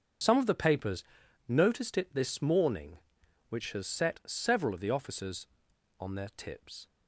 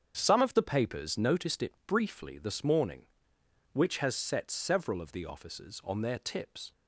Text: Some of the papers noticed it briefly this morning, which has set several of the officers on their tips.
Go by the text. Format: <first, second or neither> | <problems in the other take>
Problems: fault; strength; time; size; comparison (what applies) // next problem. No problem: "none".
second | starts louder than the rest; strong; until 1.6 s; 7 dB; strong in the second // pauses between "papers" and "noticed"; noticeable; at 1.0 s; 0.46 s long // skips "briefly"; at 2.1 s